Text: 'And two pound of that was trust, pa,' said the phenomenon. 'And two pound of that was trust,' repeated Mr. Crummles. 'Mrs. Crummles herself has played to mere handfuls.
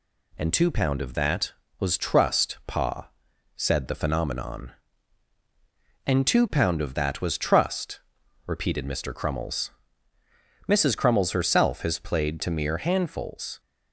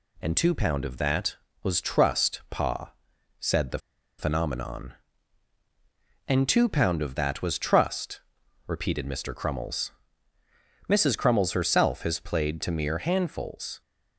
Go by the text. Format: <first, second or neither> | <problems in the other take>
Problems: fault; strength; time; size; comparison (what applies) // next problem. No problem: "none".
first | pauses between "the" and "phenomenon"; at 3.7 s; 0.40 s long